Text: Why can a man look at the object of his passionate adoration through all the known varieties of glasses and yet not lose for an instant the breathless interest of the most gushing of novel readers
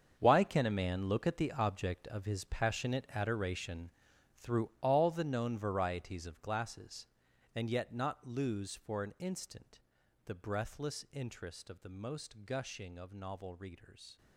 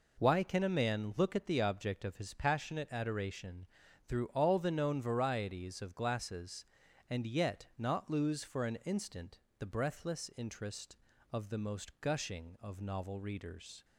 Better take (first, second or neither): second